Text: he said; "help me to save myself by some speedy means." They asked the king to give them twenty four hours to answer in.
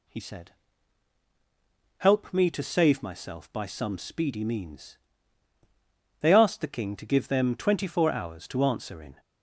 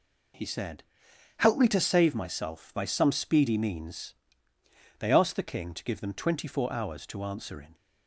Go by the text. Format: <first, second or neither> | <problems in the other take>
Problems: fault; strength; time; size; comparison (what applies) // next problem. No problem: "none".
neither | none